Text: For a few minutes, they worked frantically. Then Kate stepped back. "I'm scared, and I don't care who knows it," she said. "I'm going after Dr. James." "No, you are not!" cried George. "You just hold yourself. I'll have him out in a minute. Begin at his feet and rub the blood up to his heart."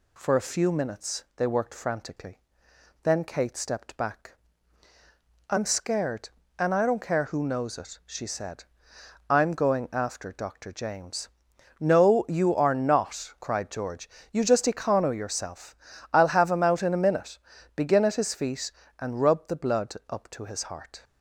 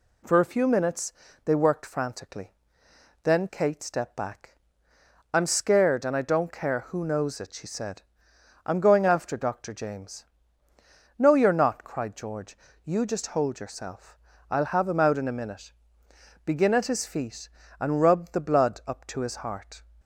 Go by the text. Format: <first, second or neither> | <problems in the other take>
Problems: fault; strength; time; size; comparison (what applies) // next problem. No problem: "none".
second | says "econo" for "hold"; at 14.6 s